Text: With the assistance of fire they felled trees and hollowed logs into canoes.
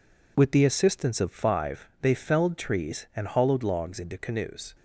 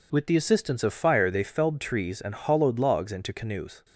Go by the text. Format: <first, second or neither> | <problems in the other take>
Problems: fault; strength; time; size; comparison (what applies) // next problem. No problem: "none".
second | says "five" for "fire"; at 1.3 s